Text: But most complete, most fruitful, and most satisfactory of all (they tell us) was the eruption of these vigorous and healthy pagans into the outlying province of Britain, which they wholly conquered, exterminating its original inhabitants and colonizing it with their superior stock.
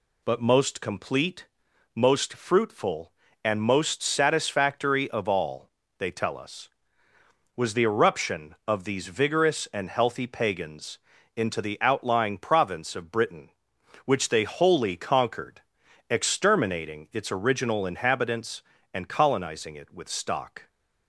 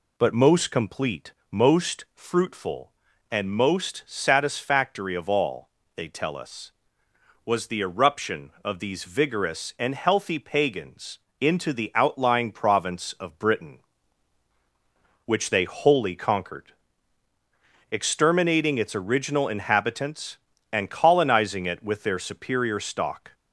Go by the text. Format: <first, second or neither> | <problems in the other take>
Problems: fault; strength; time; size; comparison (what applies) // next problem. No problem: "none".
second | pauses between "pagans" and "into"; at 10.9 s; 0.38 s long; slight in the second // skips "their superior"; at 20.0 s